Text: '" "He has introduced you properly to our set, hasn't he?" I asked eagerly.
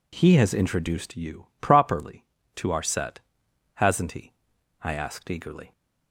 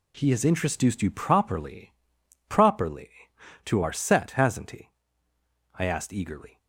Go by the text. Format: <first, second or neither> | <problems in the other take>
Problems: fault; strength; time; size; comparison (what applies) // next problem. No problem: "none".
first | says "properly" twice; at 2.4 s